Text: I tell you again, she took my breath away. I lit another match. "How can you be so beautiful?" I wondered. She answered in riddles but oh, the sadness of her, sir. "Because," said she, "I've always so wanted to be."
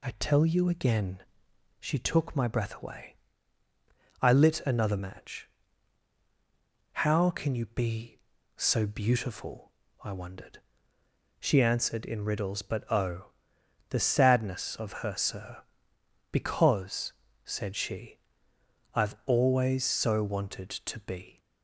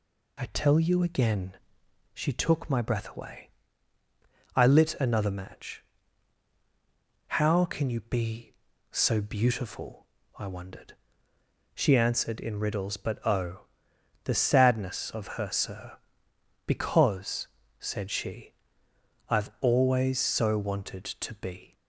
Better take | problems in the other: neither | none

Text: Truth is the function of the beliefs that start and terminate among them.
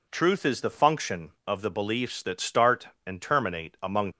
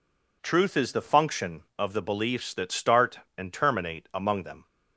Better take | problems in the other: second | stops before "them"; at 4.1 s

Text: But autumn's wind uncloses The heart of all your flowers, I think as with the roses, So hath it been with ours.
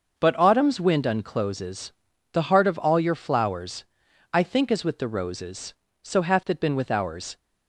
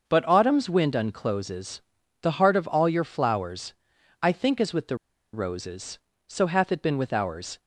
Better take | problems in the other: first | starts louder than the rest; noticeable; until 1.1 s; 6 dB; noticeable in the first // pauses between "uncloses" and "The"; at 1.7 s; 0.42 s long; also in the first // pauses between "the" and "roses"; slight; at 4.9 s; 0.35 s long

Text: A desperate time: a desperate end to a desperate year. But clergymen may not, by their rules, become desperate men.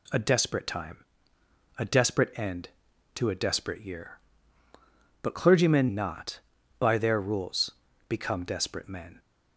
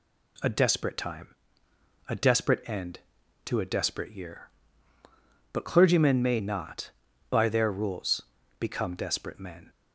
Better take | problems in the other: second | skips "may"; at 5.8 s

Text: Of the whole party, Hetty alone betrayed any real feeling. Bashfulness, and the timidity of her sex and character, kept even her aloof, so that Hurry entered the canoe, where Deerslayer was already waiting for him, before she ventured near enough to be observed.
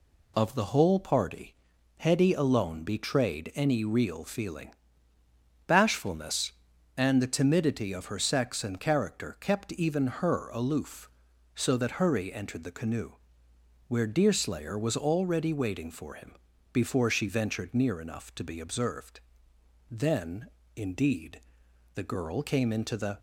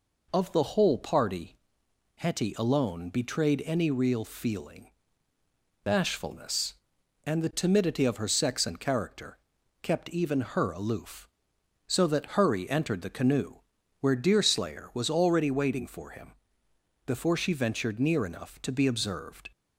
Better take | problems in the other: second | goes on to say "Then indeed the girl came into the"; strong; from 19.8 s on; 3.2 s long

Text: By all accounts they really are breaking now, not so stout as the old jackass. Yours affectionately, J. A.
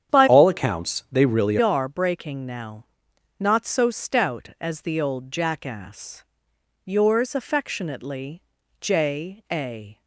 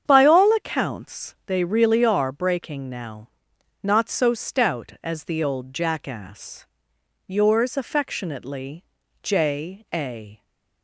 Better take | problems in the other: second | starts louder than the rest; strong; until 1.1 s; 9 dB; strong in the second // changes voice from "all" to "really"; from 0.2 to 1.5 s; 1.3 s long

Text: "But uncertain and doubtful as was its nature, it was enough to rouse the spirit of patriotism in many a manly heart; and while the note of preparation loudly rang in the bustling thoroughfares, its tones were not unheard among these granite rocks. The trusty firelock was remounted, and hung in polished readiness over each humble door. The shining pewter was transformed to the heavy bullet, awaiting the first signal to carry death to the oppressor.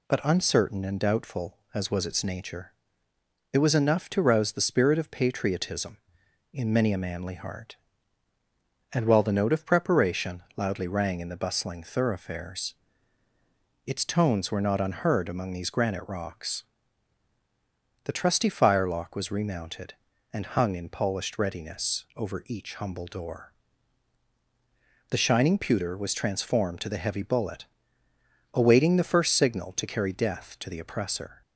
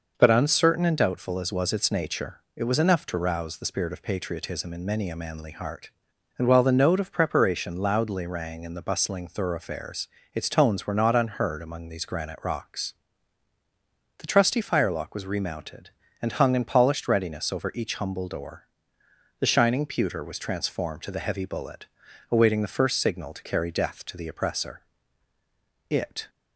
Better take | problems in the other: first | goes on to say "It"; slight; from 25.8 s on; 0.40 s long

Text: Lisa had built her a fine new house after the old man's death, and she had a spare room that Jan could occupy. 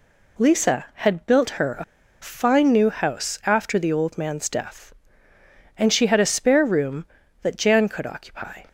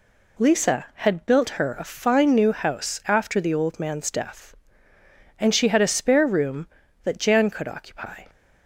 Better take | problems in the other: second | pauses between "a" and "fine"; at 1.8 s; 0.38 s long

